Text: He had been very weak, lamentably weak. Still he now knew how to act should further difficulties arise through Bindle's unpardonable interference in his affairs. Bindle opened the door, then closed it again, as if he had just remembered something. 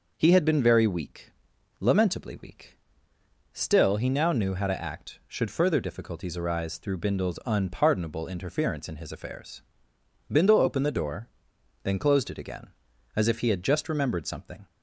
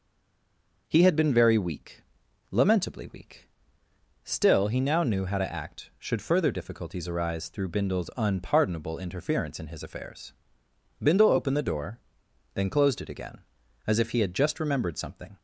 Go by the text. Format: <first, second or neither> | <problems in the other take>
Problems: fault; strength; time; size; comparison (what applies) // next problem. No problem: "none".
first | stays silent before the first word; slight; until 0.8 s; 0.8 s long